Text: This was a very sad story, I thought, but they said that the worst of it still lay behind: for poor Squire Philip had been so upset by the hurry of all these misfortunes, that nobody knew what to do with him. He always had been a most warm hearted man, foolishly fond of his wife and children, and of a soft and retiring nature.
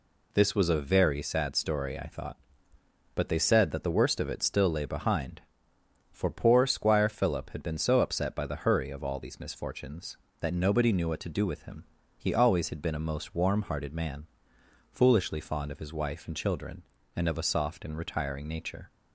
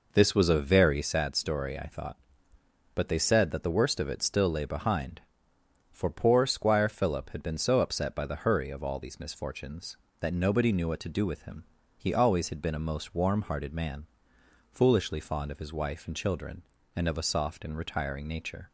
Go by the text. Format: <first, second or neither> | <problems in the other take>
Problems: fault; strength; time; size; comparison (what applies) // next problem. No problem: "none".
first | starts louder than the rest; noticeable; until 1.3 s; 4.5 dB